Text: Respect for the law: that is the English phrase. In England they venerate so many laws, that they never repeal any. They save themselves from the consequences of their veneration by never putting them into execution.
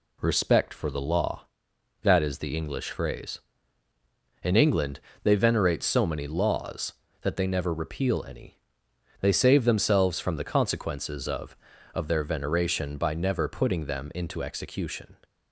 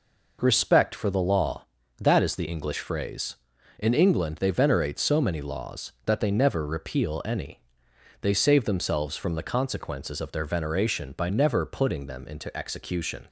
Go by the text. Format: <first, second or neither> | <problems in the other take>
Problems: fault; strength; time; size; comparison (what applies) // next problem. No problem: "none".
second | pauses between "England" and "they"; slight; at 4.9 s; 0.24 s long // says "of" twice; at 11.9 s